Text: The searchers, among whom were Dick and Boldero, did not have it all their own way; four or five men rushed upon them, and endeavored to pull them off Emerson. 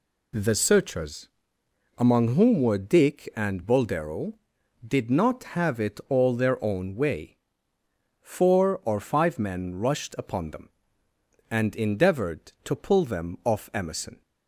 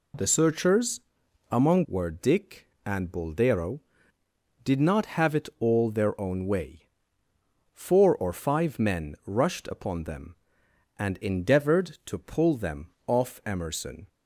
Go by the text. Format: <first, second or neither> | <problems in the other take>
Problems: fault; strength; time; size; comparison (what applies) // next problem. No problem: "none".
first | skips "whom"; at 1.8 s // pauses between "them" and "off"; slight; at 12.8 s; 0.16 s long